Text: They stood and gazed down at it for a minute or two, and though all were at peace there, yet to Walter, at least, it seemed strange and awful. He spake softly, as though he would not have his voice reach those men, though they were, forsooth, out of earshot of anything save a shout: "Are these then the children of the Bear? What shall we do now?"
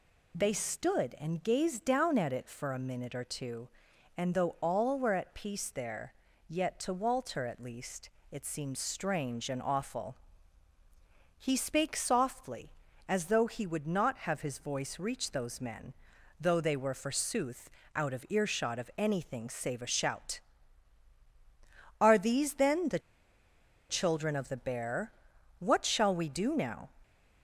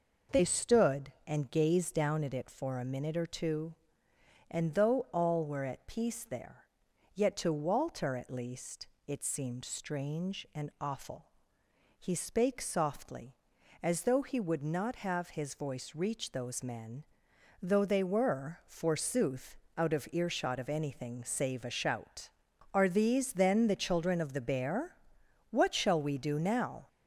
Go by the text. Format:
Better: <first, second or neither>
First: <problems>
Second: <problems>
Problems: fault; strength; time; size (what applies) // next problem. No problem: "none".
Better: second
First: pauses between "the" and "children"; noticeable; at 22.9 s; 0.89 s long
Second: none